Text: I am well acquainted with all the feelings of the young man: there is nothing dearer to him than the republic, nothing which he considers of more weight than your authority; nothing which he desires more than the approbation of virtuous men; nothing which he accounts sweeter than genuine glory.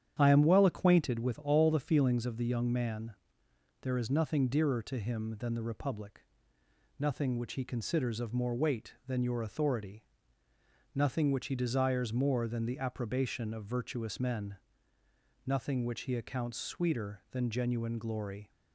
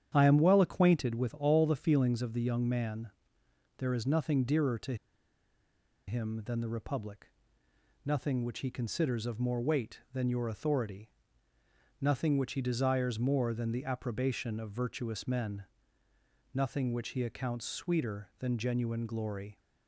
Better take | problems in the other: first | starts louder than the rest; strong; until 1.1 s; 9 dB; strong in the first // pauses between "to" and "him"; at 4.9 s; 1.1 s long

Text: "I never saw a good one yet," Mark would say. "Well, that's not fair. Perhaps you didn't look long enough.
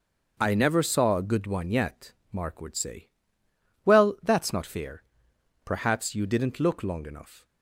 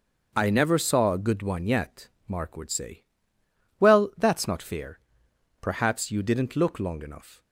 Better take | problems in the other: neither | starts louder than the rest; the same in both

